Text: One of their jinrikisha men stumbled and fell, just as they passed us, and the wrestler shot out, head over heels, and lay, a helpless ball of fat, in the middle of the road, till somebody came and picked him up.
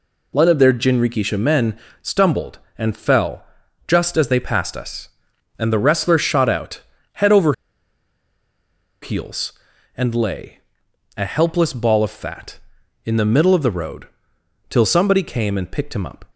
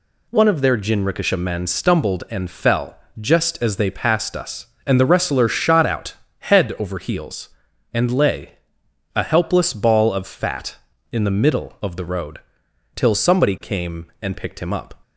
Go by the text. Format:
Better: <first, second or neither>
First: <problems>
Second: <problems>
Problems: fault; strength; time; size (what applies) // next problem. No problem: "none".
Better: second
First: pauses between "men" and "stumbled"; slight; at 1.7 s; 0.24 s long // pauses between "over" and "heels"; strong; at 7.5 s; 1.5 s long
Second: none